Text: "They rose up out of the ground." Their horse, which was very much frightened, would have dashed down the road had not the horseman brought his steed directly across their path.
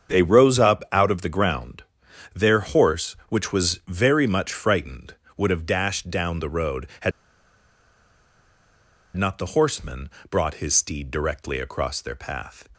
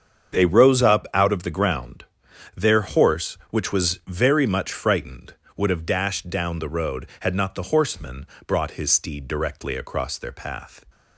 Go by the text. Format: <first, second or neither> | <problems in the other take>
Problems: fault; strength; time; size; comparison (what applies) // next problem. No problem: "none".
second | starts louder than the rest; strong; until 1.1 s; 7.5 dB; strong in the second // pauses between "had" and "not"; strong; at 7.1 s; 2.0 s long // pauses between "horseman" and "brought"; slight; at 10.1 s; 0.18 s long; slight in the second